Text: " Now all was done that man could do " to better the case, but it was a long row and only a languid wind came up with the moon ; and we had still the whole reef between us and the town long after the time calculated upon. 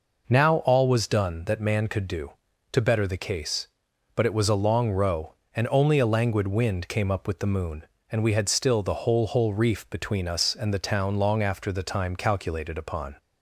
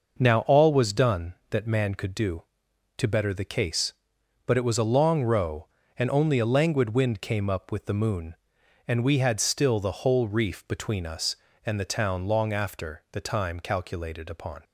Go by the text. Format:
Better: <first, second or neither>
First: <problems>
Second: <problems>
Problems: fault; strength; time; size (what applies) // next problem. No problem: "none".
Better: second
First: says "whole" twice; at 9.2 s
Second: none